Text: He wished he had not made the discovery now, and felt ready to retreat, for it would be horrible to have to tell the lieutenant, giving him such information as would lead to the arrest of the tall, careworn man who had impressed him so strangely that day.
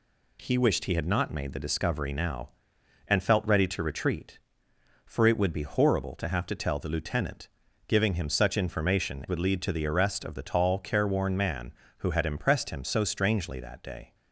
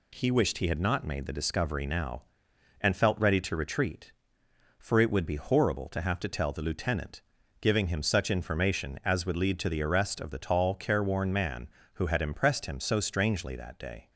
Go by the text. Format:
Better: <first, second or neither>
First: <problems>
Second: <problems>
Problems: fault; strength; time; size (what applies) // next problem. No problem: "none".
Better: second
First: skips "as"; at 9.2 s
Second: none